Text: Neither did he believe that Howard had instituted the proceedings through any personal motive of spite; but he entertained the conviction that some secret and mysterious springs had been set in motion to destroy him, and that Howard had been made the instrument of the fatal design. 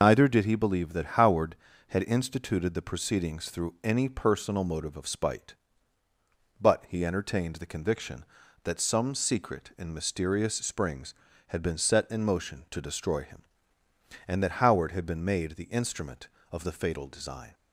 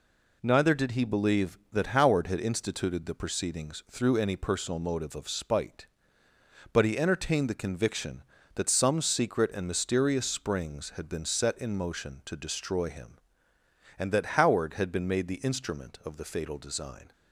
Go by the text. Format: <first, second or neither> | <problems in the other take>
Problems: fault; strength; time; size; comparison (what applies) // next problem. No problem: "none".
second | loses the start of "Neither"; at 0.0 s; 95 ms